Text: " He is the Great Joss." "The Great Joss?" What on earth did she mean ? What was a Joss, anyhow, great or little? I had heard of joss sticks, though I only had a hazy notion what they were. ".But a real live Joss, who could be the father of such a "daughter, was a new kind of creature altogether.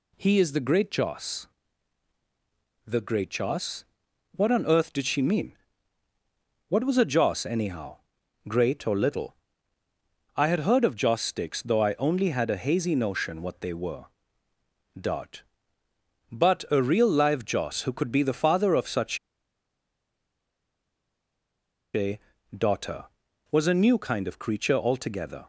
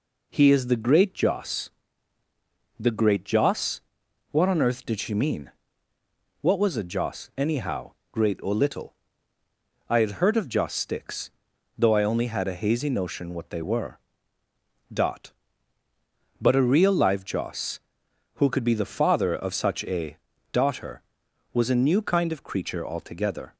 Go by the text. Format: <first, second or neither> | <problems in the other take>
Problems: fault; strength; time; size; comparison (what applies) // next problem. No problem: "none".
second | pauses between "such" and "a"; strong; at 19.1 s; 2.7 s long // pauses between "a" and "daughter"; at 22.1 s; 0.38 s long; slight in the second